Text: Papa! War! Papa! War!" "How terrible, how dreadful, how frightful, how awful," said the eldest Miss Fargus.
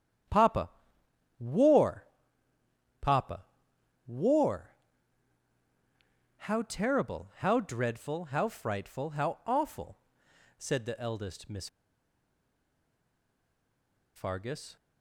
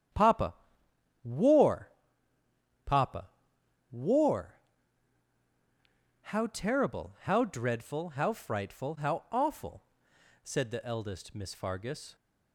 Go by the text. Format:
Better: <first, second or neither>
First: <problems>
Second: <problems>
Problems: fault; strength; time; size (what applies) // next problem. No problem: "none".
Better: second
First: starts louder than the rest; strong; until 2.0 s; 9.5 dB // pauses between "Miss" and "Fargus"; strong; at 11.6 s; 2.4 s long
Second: starts louder than the rest; strong; until 1.8 s; 9.5 dB